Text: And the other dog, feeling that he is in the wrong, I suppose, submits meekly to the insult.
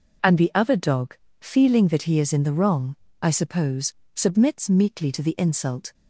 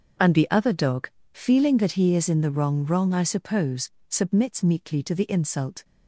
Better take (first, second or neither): first